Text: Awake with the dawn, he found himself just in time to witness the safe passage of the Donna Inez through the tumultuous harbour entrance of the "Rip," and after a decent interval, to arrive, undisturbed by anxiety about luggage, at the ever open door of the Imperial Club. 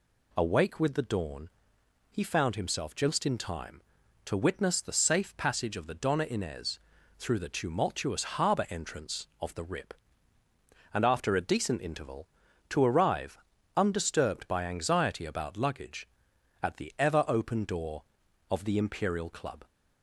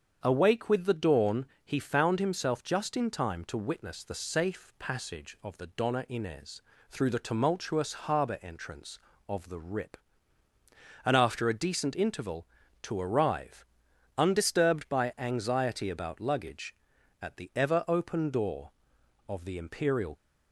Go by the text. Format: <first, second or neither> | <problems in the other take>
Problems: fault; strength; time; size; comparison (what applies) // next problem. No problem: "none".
first | starts louder than the rest; strong; until 1.2 s; 7.5 dB // pauses between "Inez" and "through"; slight; at 6.6 s; 0.30 s long; also in the first // stops before "Club"; at 20.1 s